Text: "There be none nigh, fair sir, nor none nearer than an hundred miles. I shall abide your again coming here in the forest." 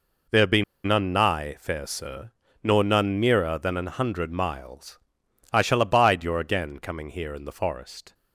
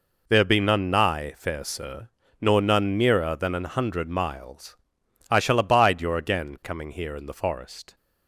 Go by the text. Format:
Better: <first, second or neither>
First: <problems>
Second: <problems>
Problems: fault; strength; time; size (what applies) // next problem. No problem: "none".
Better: second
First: pauses between "be" and "none"; slight; at 0.6 s; 0.22 s long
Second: none